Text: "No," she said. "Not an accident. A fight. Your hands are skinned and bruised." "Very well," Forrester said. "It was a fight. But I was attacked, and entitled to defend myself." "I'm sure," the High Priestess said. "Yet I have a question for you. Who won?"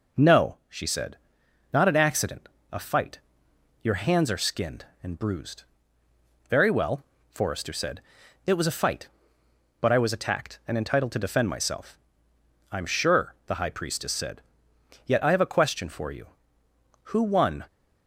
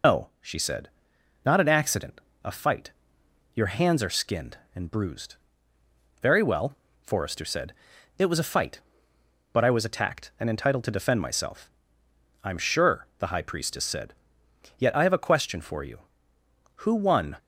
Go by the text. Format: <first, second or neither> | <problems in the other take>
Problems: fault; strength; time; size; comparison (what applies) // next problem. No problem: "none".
first | loses the start of "No"; at 0.0 s; 160 ms